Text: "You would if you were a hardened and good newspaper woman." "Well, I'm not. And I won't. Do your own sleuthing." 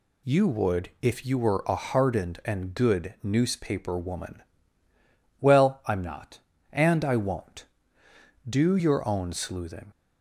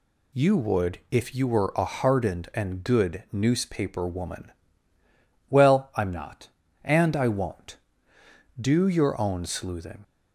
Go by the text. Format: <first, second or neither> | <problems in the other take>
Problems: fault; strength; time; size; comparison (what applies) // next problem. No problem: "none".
neither | none